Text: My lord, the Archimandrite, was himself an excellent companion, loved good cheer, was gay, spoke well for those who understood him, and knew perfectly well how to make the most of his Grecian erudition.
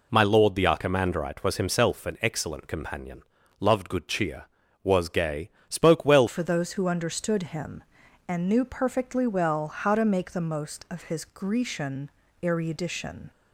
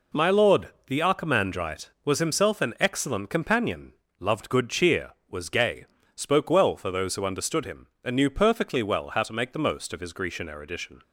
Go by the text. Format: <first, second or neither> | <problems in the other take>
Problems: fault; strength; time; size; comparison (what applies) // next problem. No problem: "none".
second | changes voice at "for"; from 6.2 s on; 7.1 s long // pauses between "Grecian" and "erudition"; slight; at 12.1 s; 0.32 s long